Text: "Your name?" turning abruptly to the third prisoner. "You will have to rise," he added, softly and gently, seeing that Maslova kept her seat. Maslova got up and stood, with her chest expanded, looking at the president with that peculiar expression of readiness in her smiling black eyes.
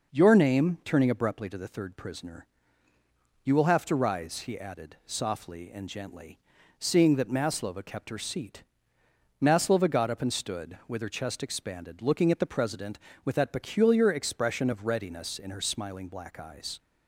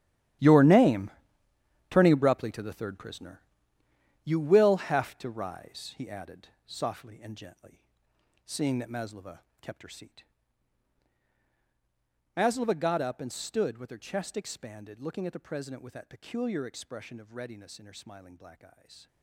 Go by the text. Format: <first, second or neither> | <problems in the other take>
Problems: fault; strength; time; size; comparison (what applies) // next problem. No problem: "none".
first | gets quieter; strong; throughout; 14.5 dB // pauses between "Maslova" and "kept"; slight; at 9.4 s; 0.18 s long